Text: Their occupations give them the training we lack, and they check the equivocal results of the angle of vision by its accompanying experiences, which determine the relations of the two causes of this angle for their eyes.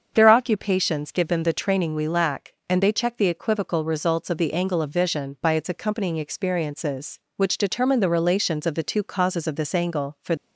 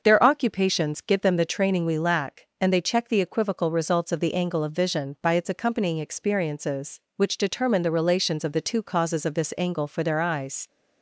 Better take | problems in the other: second | starts louder than the rest; until 1.1 s; 7 dB // stops before "their eyes"; at 10.3 s

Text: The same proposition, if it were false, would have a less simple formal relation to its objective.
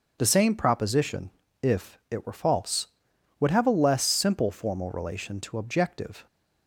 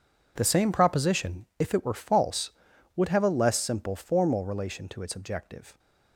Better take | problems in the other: second | starts louder than the rest; noticeable; until 1.1 s; 6 dB // skips "its"; at 5.5 s

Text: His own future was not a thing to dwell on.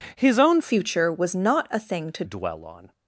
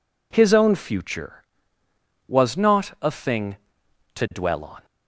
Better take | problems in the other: second | changes voice from "future" to "to"; from 0.6 to 2.2 s; 1.6 s long

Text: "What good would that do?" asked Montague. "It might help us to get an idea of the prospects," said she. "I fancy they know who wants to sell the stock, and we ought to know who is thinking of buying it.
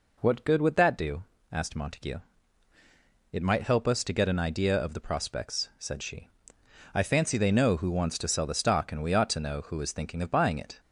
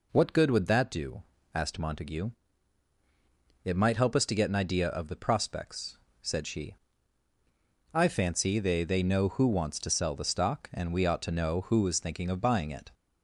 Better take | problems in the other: first | says "they" twice; at 8.8 s

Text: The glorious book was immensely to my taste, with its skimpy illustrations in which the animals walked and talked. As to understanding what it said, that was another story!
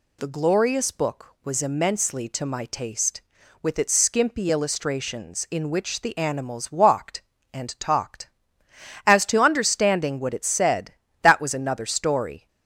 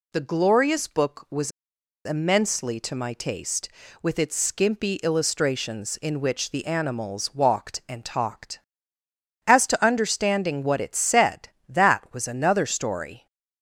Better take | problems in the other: first | pauses between "was" and "immensely"; noticeable; at 1.5 s; 0.55 s long

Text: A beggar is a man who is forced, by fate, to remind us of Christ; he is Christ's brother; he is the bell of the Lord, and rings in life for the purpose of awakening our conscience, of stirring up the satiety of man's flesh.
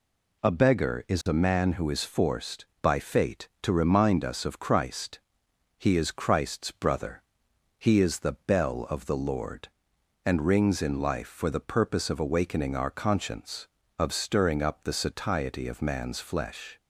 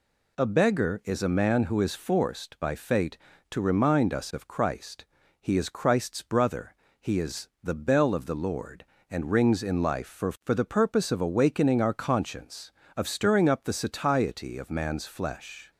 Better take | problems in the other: first | says "for" twice; at 10.4 s

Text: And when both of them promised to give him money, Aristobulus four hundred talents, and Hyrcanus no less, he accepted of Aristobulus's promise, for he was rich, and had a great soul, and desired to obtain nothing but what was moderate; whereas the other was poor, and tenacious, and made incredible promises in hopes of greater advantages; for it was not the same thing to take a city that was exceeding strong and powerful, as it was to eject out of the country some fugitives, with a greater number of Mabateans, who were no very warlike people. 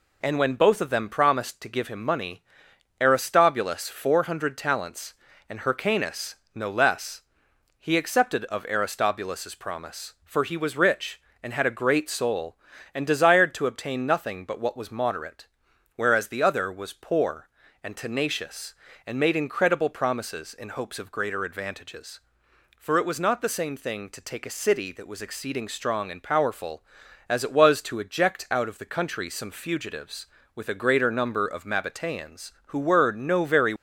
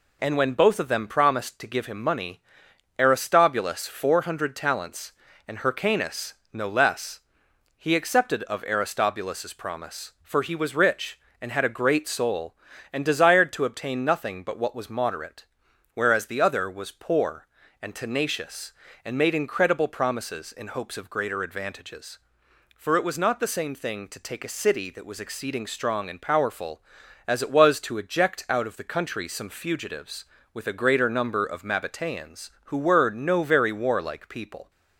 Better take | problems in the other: second | pauses between "Hyrcanus" and "no"; slight; at 6.3 s; 0.18 s long; slight in the second // stops before "warlike people"; at 33.7 s

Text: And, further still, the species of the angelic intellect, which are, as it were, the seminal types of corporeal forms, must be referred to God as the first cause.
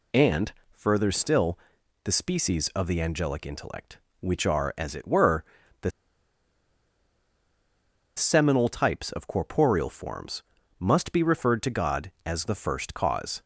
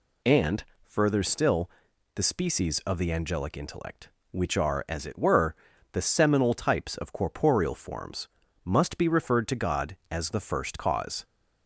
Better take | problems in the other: second | pauses between "the" and "seminal"; strong; at 5.9 s; 2.2 s long

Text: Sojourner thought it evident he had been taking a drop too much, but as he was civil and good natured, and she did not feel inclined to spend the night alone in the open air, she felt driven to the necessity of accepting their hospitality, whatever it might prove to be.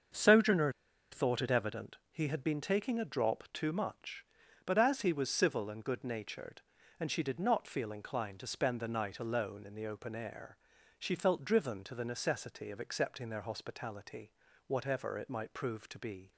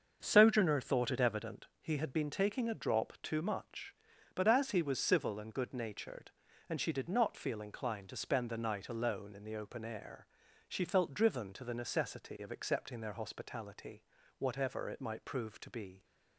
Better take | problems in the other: second | starts louder than the rest; until 1.5 s; 7 dB; also in the second // pauses between "Sojourner" and "thought"; at 0.7 s; 0.40 s long // pauses between "evident" and "he"; slight; at 1.9 s; 0.16 s long; slight in the second

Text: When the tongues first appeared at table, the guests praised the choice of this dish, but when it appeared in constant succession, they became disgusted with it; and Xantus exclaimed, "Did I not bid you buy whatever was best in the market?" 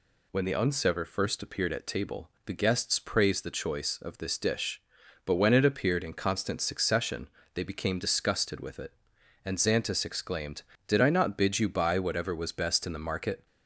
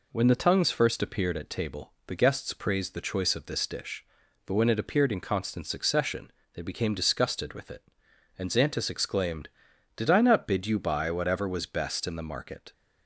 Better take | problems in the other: second | says "unsever" for "tongues"; at 0.5 s

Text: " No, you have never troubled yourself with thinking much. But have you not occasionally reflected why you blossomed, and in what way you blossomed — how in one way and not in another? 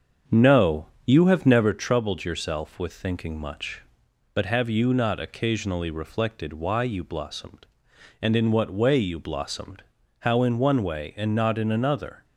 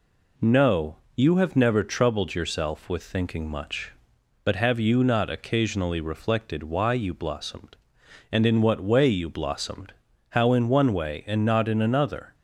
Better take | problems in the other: second | starts louder than the rest; until 1.8 s; 7 dB

